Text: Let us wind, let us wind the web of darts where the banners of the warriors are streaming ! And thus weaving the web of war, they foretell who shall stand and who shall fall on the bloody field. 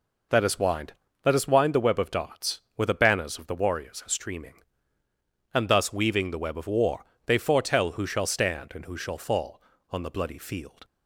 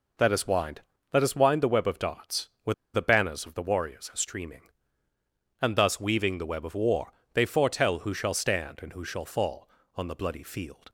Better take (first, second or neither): first